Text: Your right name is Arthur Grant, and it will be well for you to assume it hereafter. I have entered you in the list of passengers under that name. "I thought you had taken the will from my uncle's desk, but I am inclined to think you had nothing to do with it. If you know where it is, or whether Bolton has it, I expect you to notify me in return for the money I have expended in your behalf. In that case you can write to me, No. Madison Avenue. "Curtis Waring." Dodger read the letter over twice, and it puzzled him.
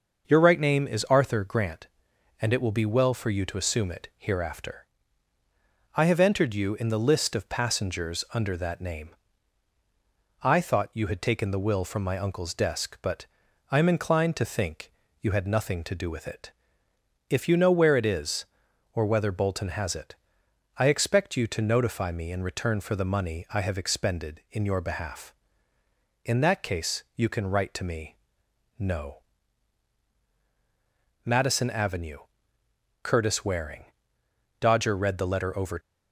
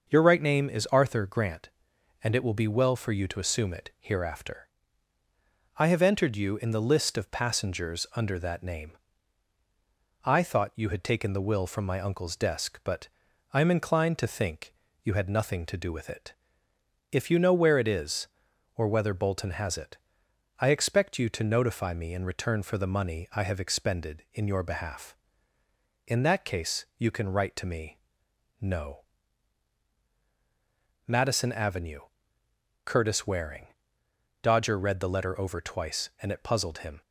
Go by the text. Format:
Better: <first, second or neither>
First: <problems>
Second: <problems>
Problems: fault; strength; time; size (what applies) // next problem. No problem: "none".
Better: second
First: starts louder than the rest; noticeable; until 1.3 s; 6 dB // pauses between "but" and "I"; at 13.2 s; 0.44 s long // pauses between "think" and "you"; slight; at 14.9 s; 0.28 s long // stops before "twice and it puzzled him"; at 35.7 s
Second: starts louder than the rest; noticeable; until 1.1 s; 6 dB // pauses between "but" and "I"; at 13.0 s; 0.44 s long // pauses between "think" and "you"; slight; at 14.7 s; 0.28 s long